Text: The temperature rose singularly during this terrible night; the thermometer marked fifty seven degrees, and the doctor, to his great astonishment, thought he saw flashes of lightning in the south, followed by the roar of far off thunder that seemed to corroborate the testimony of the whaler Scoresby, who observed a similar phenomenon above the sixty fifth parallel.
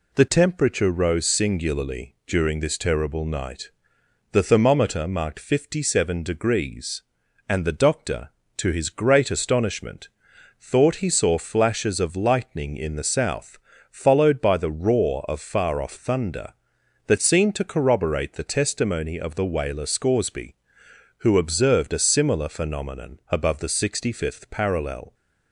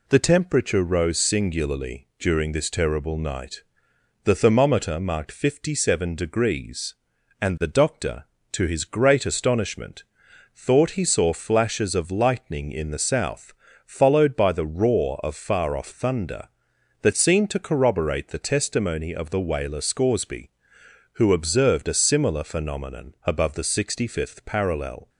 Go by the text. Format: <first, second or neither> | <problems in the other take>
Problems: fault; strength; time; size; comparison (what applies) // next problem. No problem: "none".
neither | none